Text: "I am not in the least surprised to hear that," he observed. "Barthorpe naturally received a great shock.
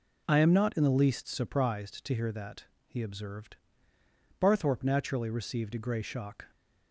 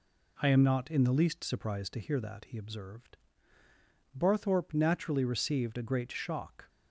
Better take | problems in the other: second | says "grey" for "great"; at 5.7 s

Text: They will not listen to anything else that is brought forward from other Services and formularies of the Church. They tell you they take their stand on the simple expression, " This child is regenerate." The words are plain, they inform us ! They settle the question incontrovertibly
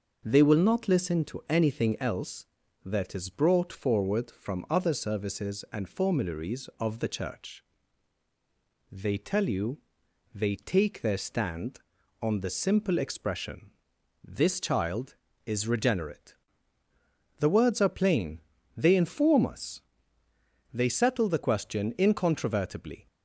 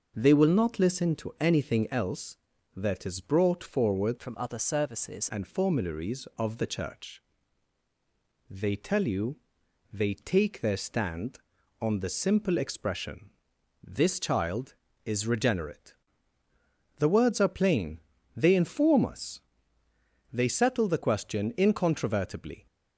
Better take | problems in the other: first | changes voice from "from" to "Services"; from 4.1 to 5.2 s; 1.1 s long // pauses between "you" and "they"; noticeable; at 9.3 s; 0.56 s long; noticeable in the first

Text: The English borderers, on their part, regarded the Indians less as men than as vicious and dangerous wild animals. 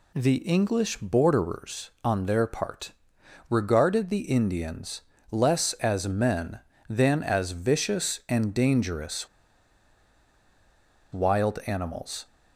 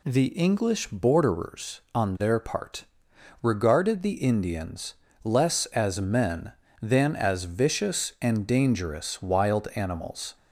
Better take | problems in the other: second | pauses between "Indians" and "less"; slight; at 5.0 s; 0.30 s long; slight in the second // pauses between "dangerous" and "wild"; strong; at 9.2 s; 1.8 s long

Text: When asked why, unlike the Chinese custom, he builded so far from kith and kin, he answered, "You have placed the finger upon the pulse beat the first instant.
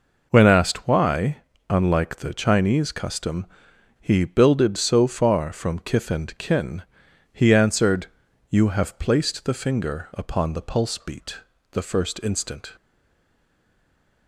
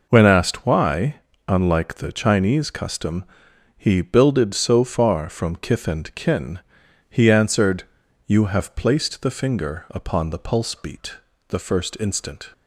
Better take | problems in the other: second | pauses between "beat" and "the"; slight; at 11.3 s; 0.32 s long; slight in the second // stays silent after the last word; noticeable; from 12.7 s on; 1.5 s long

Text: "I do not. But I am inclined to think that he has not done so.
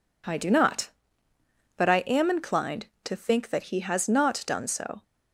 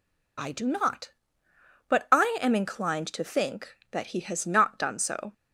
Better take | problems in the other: first | loses the start of "I"; at 0.3 s; 40 ms

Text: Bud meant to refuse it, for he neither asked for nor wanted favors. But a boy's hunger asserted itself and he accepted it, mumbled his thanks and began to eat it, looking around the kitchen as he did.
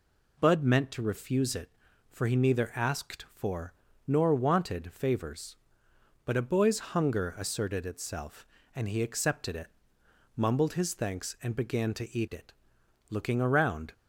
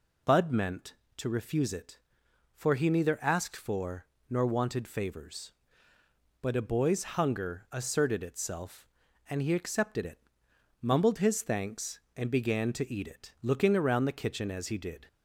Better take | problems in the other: second | pauses between "for" and "nor"; slight; at 3.7 s; 0.32 s long; slight in the second // stops before "the kitchen as he did"; at 13.9 s

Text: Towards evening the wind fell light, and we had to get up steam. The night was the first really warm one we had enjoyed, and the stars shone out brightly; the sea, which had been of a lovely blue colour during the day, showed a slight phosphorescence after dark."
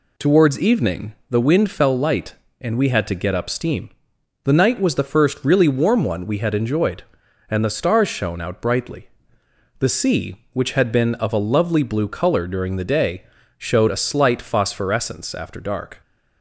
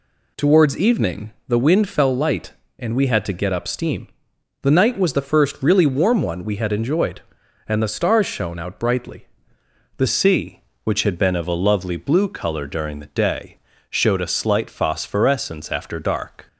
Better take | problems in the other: first | changes voice at "sea"; from 10.0 s on; 6.4 s long

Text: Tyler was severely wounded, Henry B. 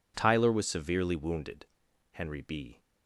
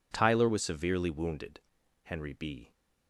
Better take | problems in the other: neither | none

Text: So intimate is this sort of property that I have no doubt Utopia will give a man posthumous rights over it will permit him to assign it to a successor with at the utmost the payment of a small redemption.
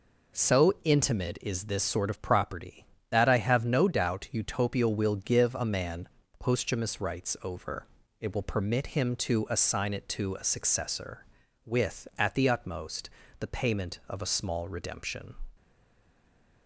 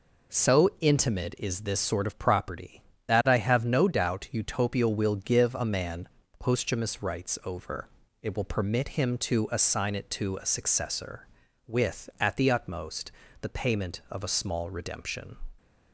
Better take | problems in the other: second | pauses between "man" and "posthumous"; slight; at 6.0 s; 0.32 s long; slight in the second // pauses between "over" and "it"; slight; at 7.8 s; 0.32 s long; slight in the second // pauses between "utmost" and "the"; slight; at 13.0 s; 0.30 s long; slight in the second // stays silent after the last word; from 15.5 s on; 1.1 s long

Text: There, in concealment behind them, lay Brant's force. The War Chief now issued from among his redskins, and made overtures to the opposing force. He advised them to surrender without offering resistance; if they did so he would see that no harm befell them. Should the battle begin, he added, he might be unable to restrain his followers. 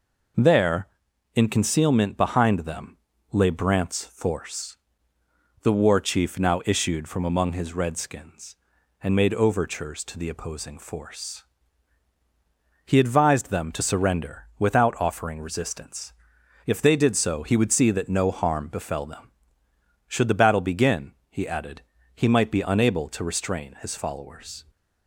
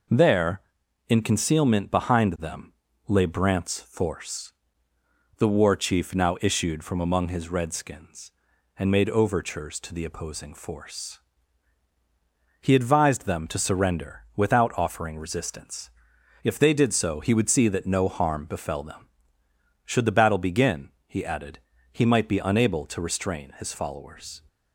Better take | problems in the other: neither | none

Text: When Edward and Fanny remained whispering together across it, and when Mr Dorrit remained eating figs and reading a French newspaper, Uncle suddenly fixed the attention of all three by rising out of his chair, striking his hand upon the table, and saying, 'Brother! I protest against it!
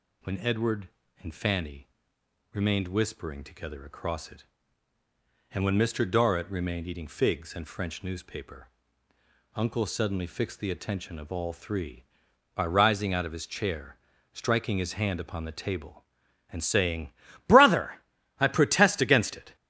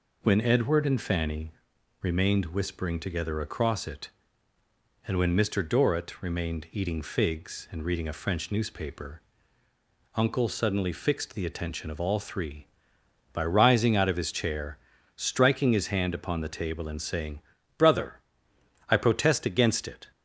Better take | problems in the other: second | pauses between "Fanny" and "remained"; noticeable; at 1.8 s; 0.66 s long; noticeable in the second // skips "reading a"; at 7.6 s

